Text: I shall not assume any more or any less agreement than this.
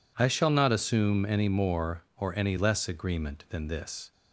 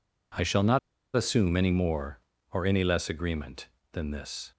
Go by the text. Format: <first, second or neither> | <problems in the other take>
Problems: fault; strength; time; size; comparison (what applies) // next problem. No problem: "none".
first | pauses between "not" and "assume"; at 0.7 s; 0.36 s long